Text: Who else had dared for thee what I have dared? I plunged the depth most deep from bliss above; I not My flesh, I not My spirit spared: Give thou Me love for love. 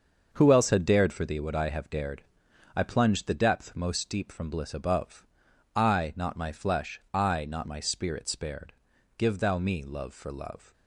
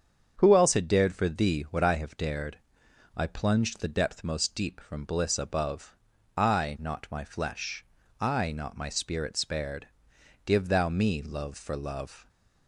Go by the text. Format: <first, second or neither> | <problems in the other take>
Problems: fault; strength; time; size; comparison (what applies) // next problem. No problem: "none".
second | gets quieter; strong; throughout; 8 dB // starts louder than the rest; until 1.3 s; 6.5 dB; strong in the second